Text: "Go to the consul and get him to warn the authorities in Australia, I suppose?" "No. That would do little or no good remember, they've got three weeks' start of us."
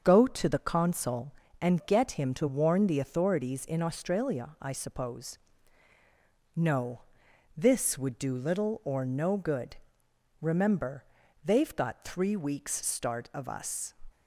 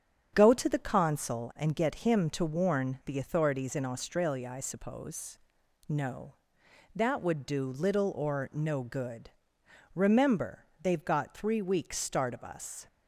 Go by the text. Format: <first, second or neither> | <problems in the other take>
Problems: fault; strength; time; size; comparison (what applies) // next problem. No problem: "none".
second | starts louder than the rest; until 1.0 s; 6.5 dB; strong in the second // says "This" for "That"; at 7.5 s // pauses between "good" and "remember"; noticeable; at 9.7 s; 0.62 s long; noticeable in the second